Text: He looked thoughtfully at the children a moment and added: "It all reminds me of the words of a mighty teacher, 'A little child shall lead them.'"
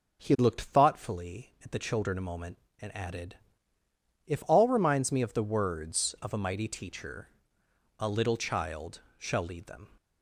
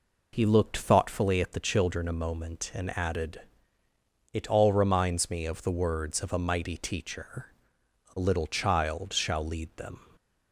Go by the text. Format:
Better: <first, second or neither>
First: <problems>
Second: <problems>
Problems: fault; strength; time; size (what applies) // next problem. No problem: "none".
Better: second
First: starts louder than the rest; noticeable; until 1.2 s; 6 dB // says "If" for "It"; at 4.2 s // pauses between "child" and "shall"; slight; at 9.0 s; 0.16 s long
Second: none